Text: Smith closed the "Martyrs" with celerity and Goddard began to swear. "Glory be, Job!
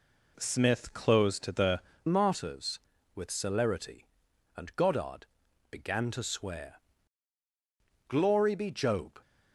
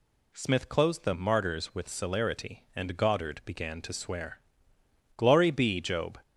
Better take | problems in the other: second | changes voice at "Martyrs"; from 2.0 s on; 7.1 s long // pauses between "Goddard" and "began"; noticeable; at 5.2 s; 0.46 s long

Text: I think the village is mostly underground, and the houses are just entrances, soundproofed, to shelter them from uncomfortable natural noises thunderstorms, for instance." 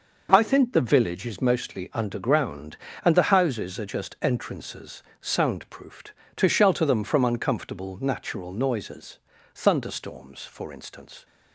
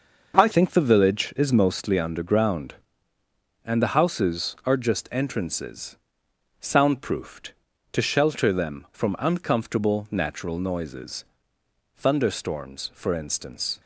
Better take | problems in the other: first | starts louder than the rest; noticeable; until 1.4 s; 6 dB // changes voice at "think"; from 0.5 s on; 13.2 s long // pauses between "noises" and "thunderstorms"; noticeable; at 11.2 s; 0.72 s long; also in the first

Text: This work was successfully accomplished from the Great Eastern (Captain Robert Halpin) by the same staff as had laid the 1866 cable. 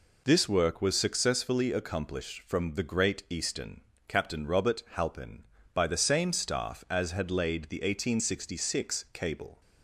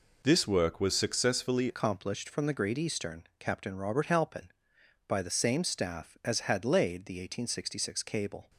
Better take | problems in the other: first | changes voice at "accomplished"; from 1.6 s on; 6.8 s long

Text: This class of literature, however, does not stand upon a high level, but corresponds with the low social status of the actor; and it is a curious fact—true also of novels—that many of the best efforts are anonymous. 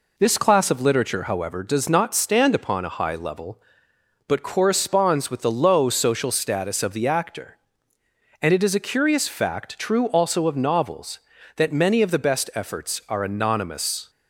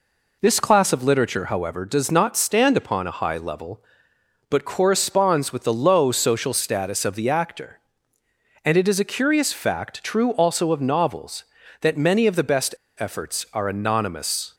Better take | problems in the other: first | pauses between "best" and "efforts"; slight; at 12.7 s; 0.25 s long

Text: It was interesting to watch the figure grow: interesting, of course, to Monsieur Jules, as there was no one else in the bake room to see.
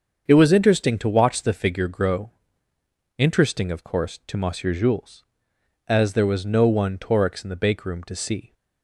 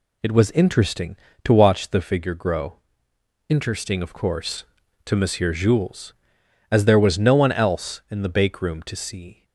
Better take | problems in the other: second | starts louder than the rest; until 1.2 s; 7 dB // says "torix" for "else"; at 6.9 s

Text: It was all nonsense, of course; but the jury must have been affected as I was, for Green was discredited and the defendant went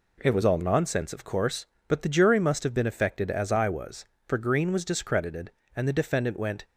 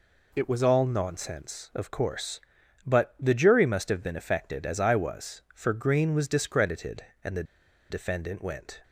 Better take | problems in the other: first | pauses between "the" and "defendant"; at 7.4 s; 0.45 s long

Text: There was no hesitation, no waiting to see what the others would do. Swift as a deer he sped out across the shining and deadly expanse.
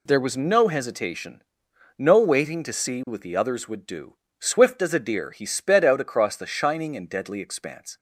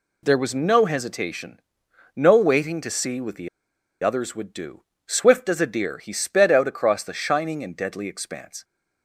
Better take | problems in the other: first | pauses between "the" and "others"; noticeable; at 3.4 s; 0.55 s long

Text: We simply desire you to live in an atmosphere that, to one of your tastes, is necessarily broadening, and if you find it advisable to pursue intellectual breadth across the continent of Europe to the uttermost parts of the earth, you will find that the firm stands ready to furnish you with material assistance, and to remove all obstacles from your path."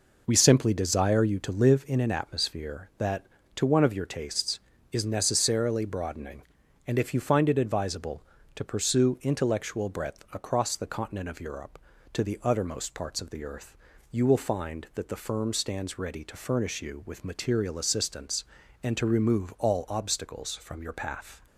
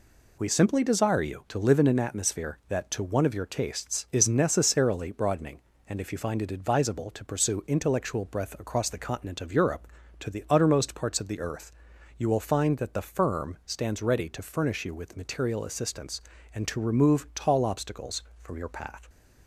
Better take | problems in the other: first | says "tall" for "all"; at 17.3 s

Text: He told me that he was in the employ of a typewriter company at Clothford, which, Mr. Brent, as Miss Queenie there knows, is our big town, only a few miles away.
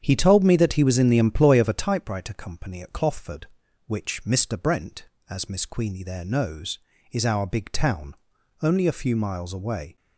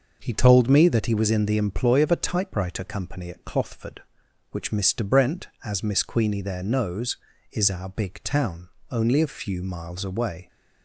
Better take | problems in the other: second | starts louder than the rest; strong; until 1.9 s; 8 dB

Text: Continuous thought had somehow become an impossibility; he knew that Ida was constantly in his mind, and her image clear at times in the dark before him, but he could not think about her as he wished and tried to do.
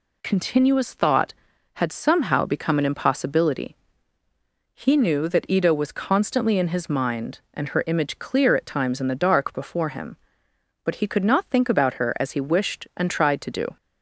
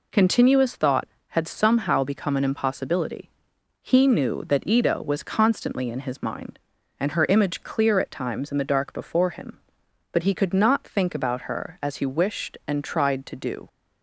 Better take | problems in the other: neither | none

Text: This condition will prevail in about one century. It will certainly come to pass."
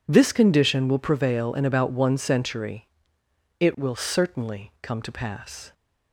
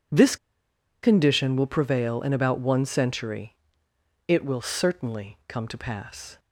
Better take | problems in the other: first | pauses between "This" and "condition"; noticeable; at 0.3 s; 0.66 s long

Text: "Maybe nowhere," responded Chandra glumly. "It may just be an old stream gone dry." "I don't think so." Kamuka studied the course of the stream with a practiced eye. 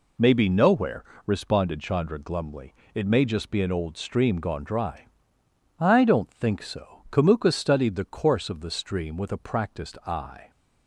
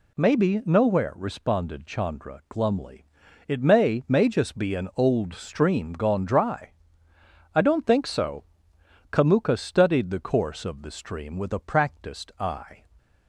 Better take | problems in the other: first | says "may" twice; at 4.0 s

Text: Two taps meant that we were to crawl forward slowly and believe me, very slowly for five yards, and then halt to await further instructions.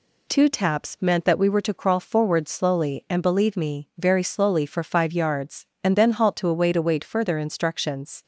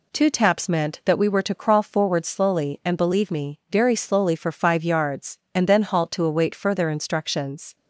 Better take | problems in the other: second | says "await" twice; at 6.7 s

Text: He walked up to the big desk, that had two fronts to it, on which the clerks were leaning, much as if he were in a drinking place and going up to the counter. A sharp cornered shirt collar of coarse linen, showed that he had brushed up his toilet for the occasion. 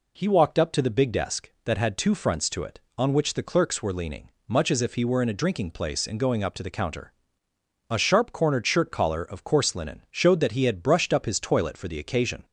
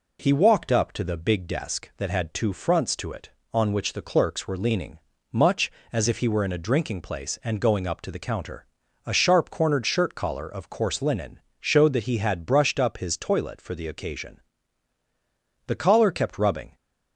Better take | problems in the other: first | goes on to say "The collar kept rubbing"; noticeable; from 15.6 s on; 1.0 s long

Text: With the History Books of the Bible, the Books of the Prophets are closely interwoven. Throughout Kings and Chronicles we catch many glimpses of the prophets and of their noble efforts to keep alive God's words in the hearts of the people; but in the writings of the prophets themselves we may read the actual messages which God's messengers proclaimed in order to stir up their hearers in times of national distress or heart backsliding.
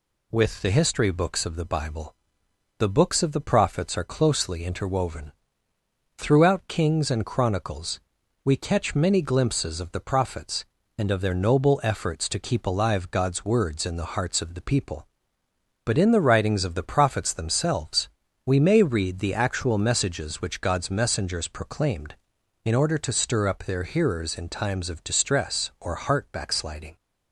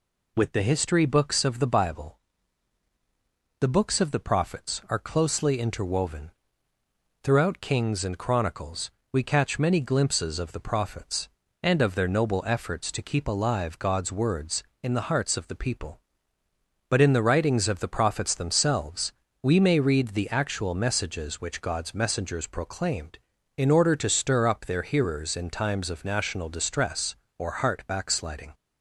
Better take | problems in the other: second | pauses between "Chronicles" and "we"; noticeable; at 7.9 s; 0.46 s long; slight in the second // pauses between "themselves" and "we"; at 18.0 s; 0.38 s long; slight in the second // skips "national"; at 25.0 s

